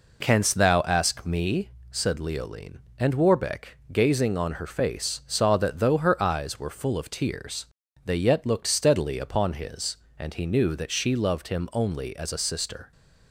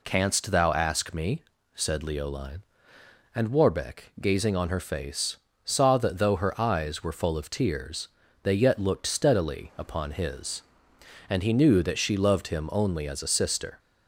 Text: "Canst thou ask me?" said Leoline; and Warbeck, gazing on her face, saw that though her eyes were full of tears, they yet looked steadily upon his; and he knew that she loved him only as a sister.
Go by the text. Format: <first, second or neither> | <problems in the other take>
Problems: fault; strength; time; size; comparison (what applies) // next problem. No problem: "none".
neither | none